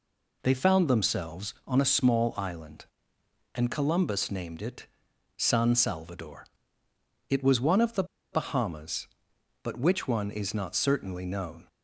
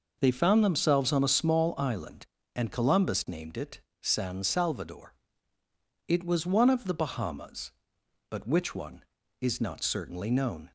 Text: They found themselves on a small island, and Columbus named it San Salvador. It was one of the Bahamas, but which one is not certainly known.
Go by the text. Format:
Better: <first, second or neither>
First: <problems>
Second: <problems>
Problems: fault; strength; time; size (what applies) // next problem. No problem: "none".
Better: second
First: pauses between "it" and "San"; noticeable; at 4.8 s; 0.50 s long // pauses between "the" and "Bahamas"; slight; at 8.0 s; 0.28 s long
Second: pauses between "it" and "San"; slight; at 3.7 s; 0.22 s long